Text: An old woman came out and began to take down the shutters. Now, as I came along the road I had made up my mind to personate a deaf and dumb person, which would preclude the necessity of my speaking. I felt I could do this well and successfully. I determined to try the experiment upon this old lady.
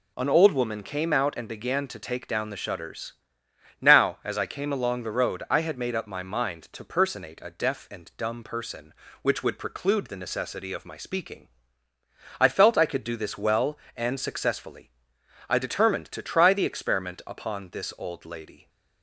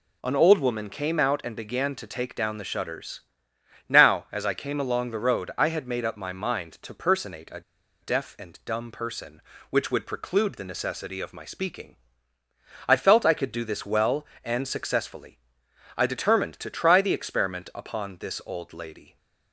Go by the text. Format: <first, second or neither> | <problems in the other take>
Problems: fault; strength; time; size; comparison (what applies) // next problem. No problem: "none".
first | pauses between "a" and "deaf"; at 7.6 s; 0.39 s long